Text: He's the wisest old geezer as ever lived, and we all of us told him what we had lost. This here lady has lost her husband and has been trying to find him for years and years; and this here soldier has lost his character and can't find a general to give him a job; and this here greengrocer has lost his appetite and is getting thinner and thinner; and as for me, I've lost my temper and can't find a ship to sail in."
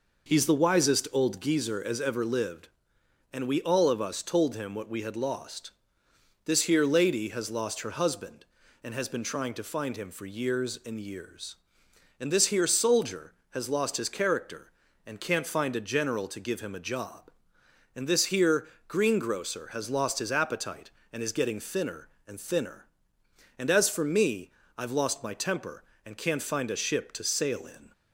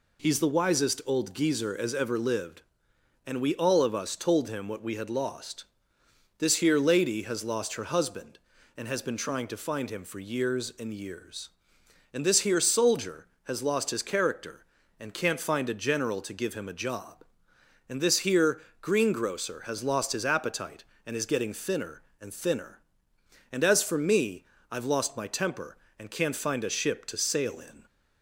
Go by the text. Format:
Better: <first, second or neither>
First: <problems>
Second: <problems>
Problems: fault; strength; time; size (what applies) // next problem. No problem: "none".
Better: second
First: starts louder than the rest; noticeable; until 1.5 s; 5.5 dB // pauses between "here" and "greengrocer"; slight; at 18.6 s; 0.22 s long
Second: pauses between "here" and "greengrocer"; slight; at 18.6 s; 0.22 s long